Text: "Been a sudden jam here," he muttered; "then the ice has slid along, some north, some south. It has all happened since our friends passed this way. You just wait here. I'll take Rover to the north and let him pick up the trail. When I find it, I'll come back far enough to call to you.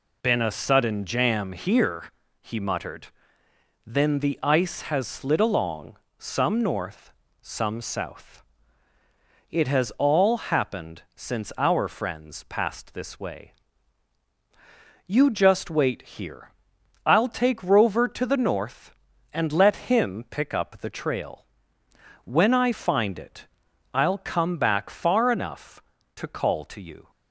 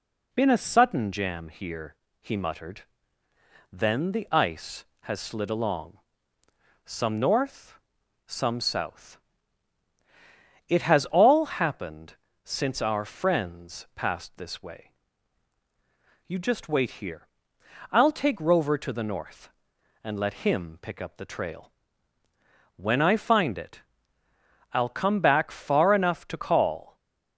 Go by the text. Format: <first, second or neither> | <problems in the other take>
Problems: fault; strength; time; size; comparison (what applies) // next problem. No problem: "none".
first | pauses between "happened" and "since"; slight; at 12.1 s; 0.30 s long // stops before "to you"; at 26.9 s